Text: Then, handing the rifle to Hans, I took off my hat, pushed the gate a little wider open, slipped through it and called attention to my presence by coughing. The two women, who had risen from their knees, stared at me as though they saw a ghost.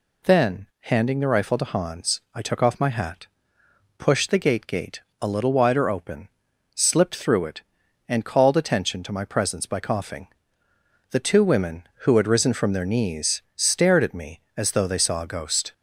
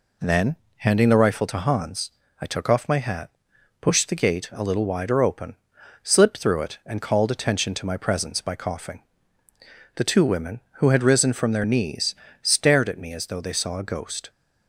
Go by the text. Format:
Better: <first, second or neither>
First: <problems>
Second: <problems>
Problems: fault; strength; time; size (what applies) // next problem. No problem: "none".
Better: second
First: says "gate" twice; at 4.6 s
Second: none